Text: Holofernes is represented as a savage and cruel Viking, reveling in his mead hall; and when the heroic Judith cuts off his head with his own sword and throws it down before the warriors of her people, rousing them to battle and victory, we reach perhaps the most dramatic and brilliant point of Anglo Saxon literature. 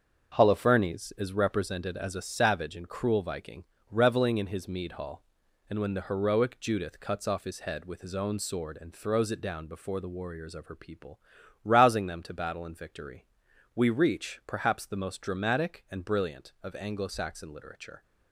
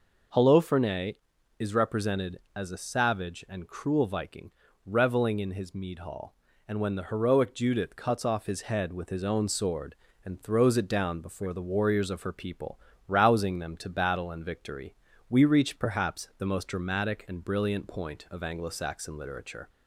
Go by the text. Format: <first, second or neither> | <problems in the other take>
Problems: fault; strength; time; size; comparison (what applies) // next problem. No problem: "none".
second | starts louder than the rest; until 1.3 s; 6.5 dB // skips "point"; at 16.5 s